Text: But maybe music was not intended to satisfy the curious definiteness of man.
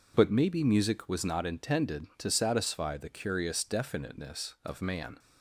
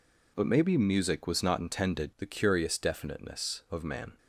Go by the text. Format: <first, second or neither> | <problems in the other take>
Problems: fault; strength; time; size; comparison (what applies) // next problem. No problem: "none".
first | skips "to satisfy"; at 2.1 s